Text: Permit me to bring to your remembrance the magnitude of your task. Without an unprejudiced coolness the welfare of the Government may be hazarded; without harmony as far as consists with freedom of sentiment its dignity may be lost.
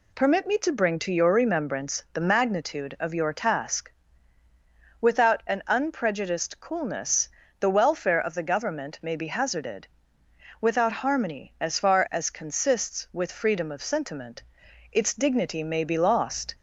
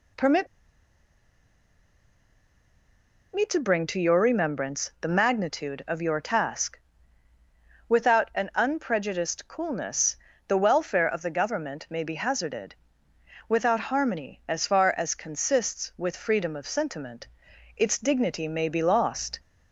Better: first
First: pauses between "coolness" and "the"; slight; at 7.3 s; 0.30 s long // pauses between "sentiment" and "its"; noticeable; at 14.4 s; 0.52 s long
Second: pauses between "Permit" and "me"; strong; at 0.4 s; 2.8 s long // pauses between "coolness" and "the"; slight; at 10.1 s; 0.30 s long // pauses between "sentiment" and "its"; noticeable; at 17.2 s; 0.52 s long

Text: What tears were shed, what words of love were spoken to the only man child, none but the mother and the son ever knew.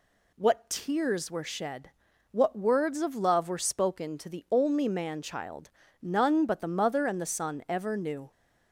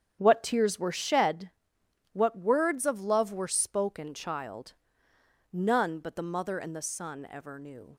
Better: first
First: none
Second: starts louder than the rest; strong; until 1.2 s; 8.5 dB // skips "to the only man"; at 4.1 s

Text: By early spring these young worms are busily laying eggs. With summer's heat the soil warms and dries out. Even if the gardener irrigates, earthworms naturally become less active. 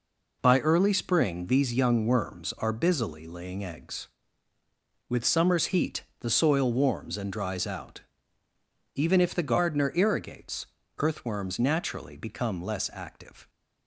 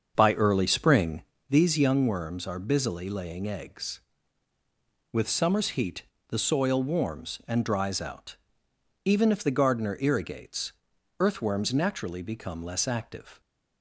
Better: first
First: pauses between "heat" and "the"; slight; at 6.0 s; 0.18 s long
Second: starts louder than the rest; until 1.5 s; 6.5 dB // pauses between "spring" and "these"; slight; at 1.2 s; 0.30 s long // pauses between "heat" and "the"; slight; at 6.0 s; 0.24 s long

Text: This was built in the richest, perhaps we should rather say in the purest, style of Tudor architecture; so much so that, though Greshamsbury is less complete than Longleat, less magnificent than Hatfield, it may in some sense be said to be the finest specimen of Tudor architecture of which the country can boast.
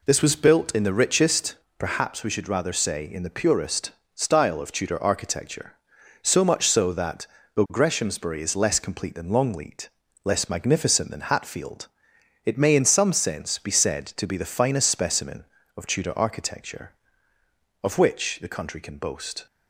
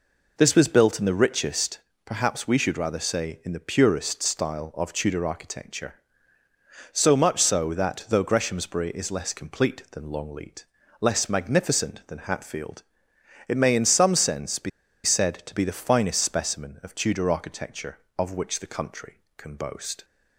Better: first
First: none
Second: pauses between "be" and "said"; slight; at 14.6 s; 0.35 s long

